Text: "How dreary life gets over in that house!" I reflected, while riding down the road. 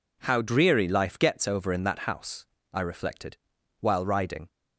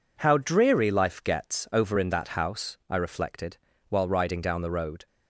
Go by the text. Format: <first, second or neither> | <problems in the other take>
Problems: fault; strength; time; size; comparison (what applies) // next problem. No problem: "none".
second | stops before "down the road"; at 4.4 s